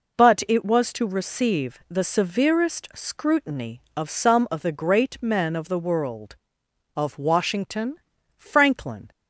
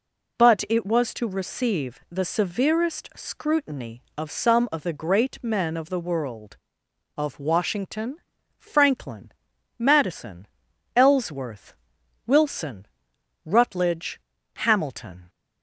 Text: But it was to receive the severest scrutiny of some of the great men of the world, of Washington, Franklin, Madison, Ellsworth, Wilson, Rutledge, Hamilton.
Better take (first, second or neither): second